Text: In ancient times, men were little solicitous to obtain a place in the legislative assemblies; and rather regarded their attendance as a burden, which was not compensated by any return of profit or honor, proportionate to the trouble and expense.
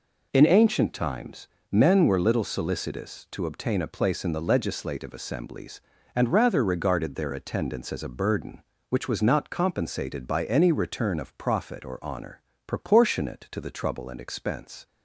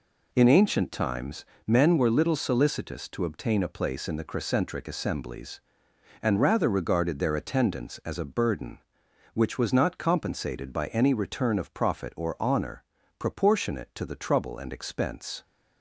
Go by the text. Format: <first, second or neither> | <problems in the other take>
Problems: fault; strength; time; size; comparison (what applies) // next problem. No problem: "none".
first | says "crescentric" for "legislative"; at 4.2 s